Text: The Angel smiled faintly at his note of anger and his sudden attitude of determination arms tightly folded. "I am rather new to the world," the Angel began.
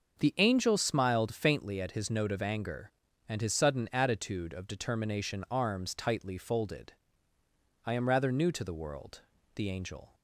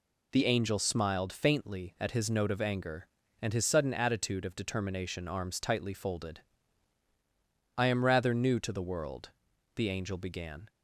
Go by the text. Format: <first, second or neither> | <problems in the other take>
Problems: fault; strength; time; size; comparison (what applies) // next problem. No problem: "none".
second | starts louder than the rest; until 1.2 s; 6 dB // stops before "began"; at 10.1 s